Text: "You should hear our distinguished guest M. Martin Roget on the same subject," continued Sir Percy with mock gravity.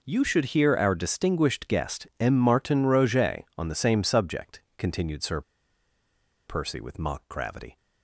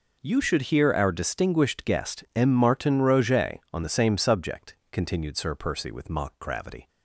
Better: second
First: pauses between "Sir" and "Percy"; at 5.4 s; 1.0 s long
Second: none

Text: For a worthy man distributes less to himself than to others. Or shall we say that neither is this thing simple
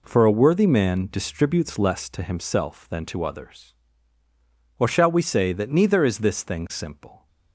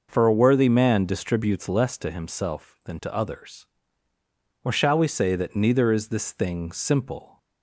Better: neither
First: none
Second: none

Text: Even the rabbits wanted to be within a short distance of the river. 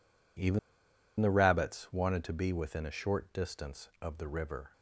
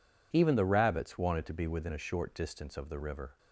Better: second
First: pauses between "Even" and "the"; noticeable; at 0.5 s; 0.60 s long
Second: none

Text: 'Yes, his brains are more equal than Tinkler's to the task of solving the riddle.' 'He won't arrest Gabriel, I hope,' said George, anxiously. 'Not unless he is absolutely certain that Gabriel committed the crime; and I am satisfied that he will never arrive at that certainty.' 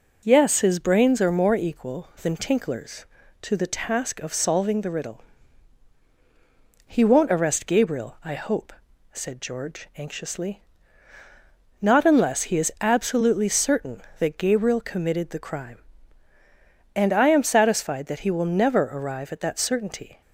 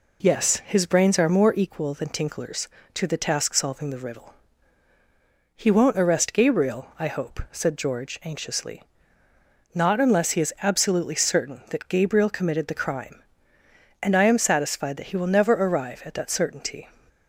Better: first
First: none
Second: skips "of"; at 3.5 s

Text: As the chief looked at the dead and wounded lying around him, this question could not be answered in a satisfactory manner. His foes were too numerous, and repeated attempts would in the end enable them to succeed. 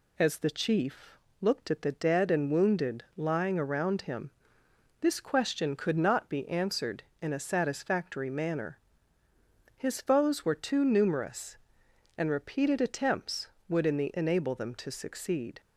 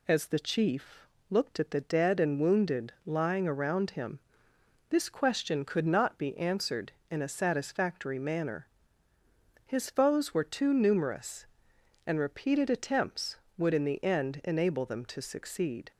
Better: second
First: pauses between "chief" and "looked"; slight; at 1.1 s; 0.24 s long // skips "end"; at 14.1 s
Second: pauses between "chief" and "looked"; slight; at 1.0 s; 0.24 s long

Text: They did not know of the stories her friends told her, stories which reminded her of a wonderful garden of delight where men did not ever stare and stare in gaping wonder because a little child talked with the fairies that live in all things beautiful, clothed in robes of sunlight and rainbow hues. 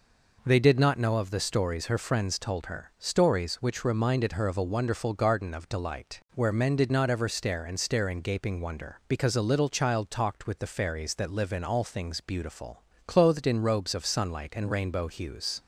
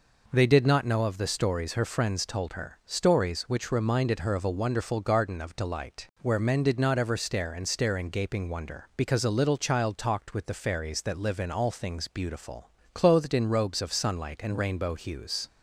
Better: neither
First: none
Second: none

